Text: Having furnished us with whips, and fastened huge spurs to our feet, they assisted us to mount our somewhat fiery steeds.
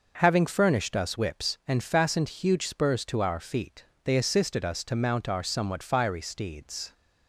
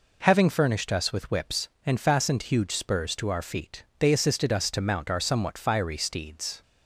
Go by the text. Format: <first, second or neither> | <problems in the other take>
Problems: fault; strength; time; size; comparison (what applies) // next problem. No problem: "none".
second | skips "with"; at 1.1 s